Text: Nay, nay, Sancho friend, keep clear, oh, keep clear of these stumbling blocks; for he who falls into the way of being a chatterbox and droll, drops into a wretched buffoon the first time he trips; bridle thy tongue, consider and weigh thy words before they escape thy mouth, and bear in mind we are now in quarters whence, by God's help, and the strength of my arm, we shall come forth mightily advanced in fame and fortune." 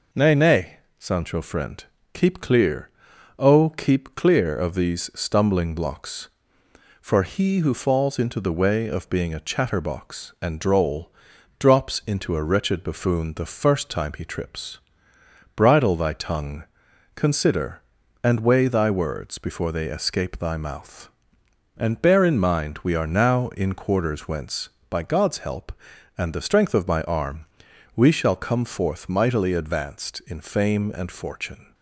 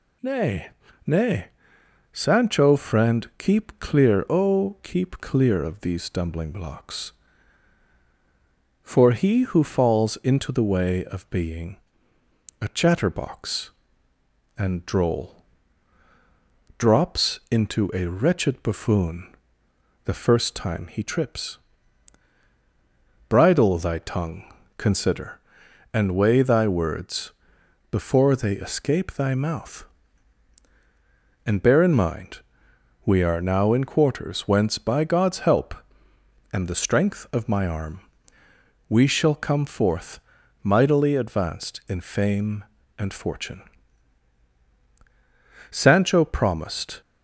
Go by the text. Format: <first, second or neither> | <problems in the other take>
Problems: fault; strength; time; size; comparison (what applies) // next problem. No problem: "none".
first | pauses between "being" and "a"; noticeable; at 11.7 s; 0.84 s long // pauses between "buffoon" and "the"; noticeable; at 19.3 s; 0.70 s long // pauses between "words" and "before"; noticeable; at 27.3 s; 0.62 s long // pauses between "mind" and "we"; noticeable; at 32.4 s; 0.64 s long // pauses between "forth" and "mightily"; at 40.1 s; 0.44 s long // goes on to say "Sancho promised"; noticeable; from 45.7 s on; 1.3 s long